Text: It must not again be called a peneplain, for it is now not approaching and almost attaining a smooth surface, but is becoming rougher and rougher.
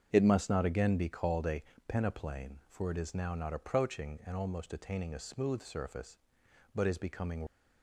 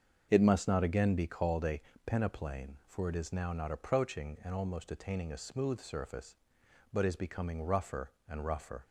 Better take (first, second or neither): second